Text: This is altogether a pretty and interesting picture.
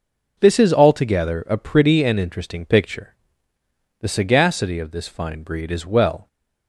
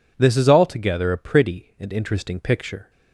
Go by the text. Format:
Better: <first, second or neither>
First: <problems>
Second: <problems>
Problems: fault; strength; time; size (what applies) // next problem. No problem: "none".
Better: second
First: goes on to say "The sagacity of this fine breed is well"; strong; from 4.0 s on; 2.2 s long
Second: none